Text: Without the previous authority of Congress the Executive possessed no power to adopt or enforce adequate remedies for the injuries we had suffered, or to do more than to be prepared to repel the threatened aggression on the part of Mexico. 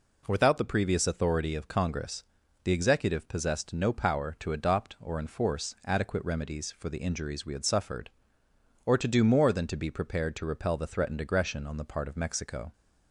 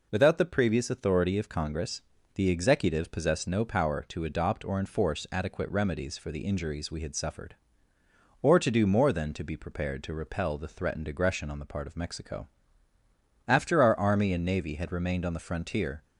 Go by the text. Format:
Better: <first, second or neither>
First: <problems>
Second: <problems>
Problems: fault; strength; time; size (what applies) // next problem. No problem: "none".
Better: first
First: pauses between "Congress" and "the"; at 2.2 s; 0.40 s long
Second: pauses between "Congress" and "the"; slight; at 2.0 s; 0.34 s long // goes on to say "After our Army and Navy had remained on the frontier"; strong; from 13.4 s on; 2.5 s long